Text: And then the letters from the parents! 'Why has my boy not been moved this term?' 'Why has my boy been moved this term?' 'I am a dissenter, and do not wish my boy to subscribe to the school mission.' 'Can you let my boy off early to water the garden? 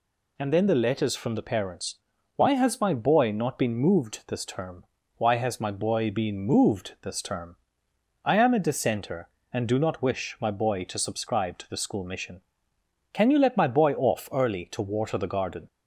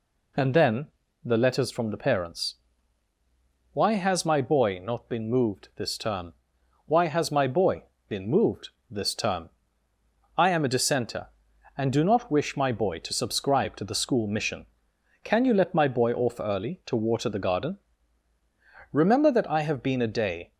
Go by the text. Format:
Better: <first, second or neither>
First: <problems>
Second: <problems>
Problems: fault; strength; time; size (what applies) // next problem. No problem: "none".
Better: first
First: none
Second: pauses between "then" and "the"; slight; at 0.8 s; 0.36 s long // pauses between "boy" and "been"; slight; at 7.8 s; 0.24 s long // pauses between "moved" and "this"; slight; at 8.6 s; 0.20 s long // goes on to say "Remember that I have been a day"; from 18.9 s on; 1.6 s long